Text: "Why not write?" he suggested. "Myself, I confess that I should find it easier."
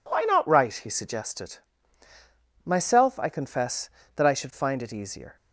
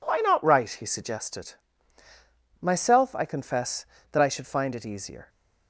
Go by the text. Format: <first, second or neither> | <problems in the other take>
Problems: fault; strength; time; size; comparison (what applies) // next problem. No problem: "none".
neither | none